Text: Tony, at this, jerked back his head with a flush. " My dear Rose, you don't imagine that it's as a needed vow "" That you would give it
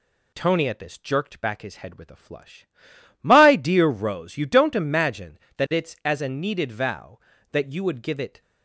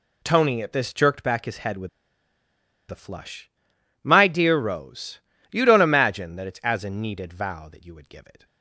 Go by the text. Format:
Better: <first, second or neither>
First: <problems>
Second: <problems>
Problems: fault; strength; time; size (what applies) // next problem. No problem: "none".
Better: first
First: none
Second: pauses between "with" and "a"; at 1.8 s; 1.0 s long